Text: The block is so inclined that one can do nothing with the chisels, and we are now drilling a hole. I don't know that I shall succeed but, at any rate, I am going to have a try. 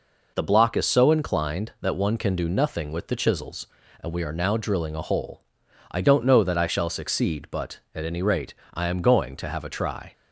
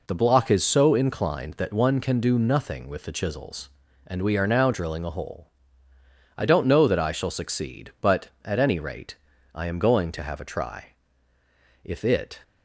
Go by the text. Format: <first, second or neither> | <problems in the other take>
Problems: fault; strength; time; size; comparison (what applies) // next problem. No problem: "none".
first | goes on to say "If it"; from 11.8 s on; 0.56 s long